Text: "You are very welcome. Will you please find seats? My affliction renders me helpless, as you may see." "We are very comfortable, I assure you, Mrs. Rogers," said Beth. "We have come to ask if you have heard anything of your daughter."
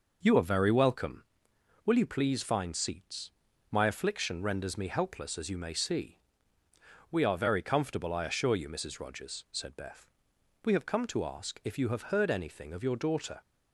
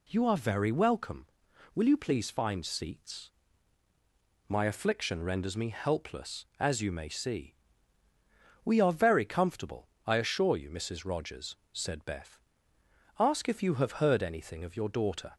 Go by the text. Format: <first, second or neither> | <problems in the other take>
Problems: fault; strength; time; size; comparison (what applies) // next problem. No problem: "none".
first | skips "We have come to"; at 12.7 s